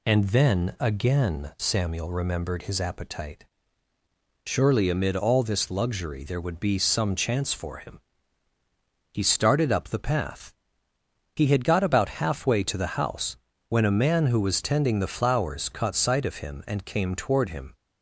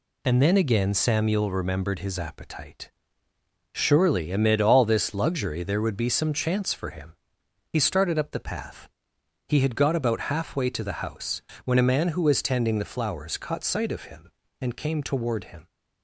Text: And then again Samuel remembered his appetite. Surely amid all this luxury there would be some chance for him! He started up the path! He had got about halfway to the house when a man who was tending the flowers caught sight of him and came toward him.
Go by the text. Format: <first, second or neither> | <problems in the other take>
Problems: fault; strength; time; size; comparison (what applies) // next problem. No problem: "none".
neither | pauses between "house" and "when"; slight; the same in both